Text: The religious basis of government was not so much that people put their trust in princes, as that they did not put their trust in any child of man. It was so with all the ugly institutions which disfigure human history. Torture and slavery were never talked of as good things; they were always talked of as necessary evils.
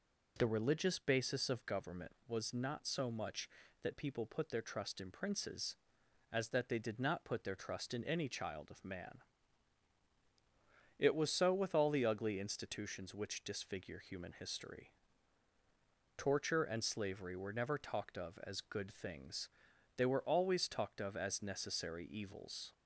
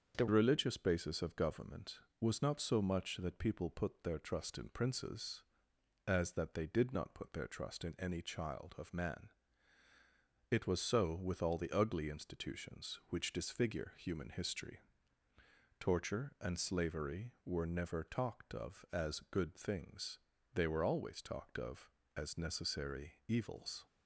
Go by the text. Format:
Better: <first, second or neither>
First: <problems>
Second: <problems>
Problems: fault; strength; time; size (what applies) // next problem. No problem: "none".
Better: first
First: none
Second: starts louder than the rest; until 1.2 s; 7 dB // changes voice at "religious"; from 0.2 s on; 23.6 s long